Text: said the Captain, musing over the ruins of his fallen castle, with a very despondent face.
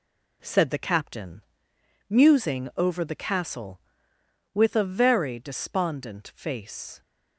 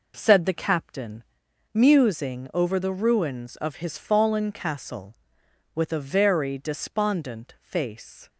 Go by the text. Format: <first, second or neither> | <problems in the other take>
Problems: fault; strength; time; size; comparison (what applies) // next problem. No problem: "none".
second | skips "ruins of his fallen"; at 3.1 s